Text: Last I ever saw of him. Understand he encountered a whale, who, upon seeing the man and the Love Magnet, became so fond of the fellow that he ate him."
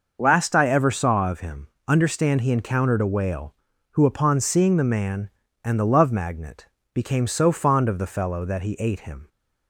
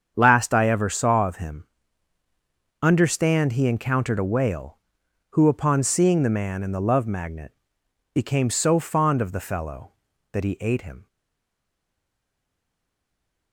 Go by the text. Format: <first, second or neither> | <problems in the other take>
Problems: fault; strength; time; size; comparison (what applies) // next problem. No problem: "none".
first | starts louder than the rest; strong; until 1.1 s; 7.5 dB // stays silent after the last word; from 11.0 s on; 2.5 s long